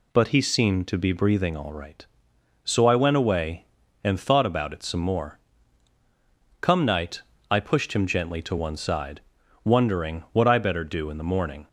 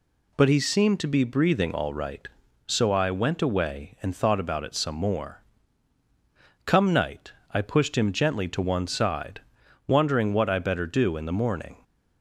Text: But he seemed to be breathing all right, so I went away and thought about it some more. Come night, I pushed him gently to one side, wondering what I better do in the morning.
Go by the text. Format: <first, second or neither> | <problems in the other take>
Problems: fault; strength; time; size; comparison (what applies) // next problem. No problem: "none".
neither | none